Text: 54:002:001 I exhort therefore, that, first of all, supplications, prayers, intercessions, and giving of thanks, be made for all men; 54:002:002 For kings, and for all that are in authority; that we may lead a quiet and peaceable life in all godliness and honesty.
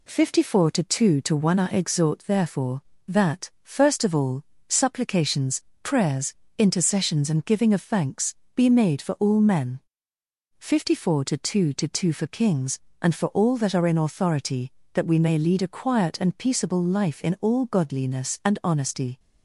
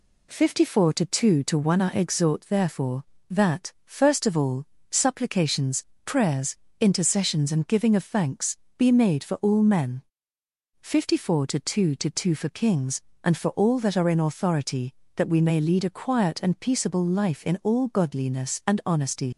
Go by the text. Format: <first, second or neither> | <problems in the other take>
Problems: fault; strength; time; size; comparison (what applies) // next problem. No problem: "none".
first | leaves "honesty" unfinished; at 19.3 s; 85 ms